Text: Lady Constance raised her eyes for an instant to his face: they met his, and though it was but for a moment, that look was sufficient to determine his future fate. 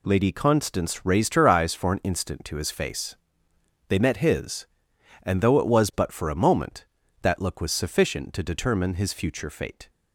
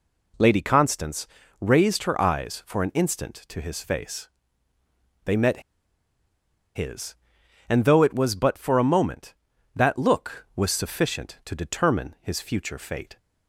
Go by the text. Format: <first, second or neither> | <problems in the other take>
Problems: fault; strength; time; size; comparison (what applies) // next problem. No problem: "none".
first | pauses between "Constance" and "raised"; slight; at 1.2 s; 0.34 s long // pauses between "met" and "his"; at 5.6 s; 1.1 s long